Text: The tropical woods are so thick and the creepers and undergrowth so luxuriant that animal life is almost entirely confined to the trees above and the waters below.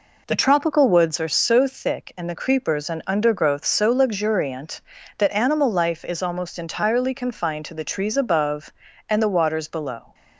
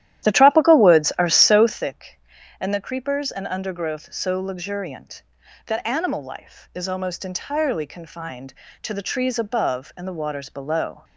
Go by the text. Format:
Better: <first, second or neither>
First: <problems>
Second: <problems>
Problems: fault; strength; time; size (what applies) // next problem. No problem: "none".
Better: first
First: none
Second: starts louder than the rest; strong; until 1.9 s; 12.5 dB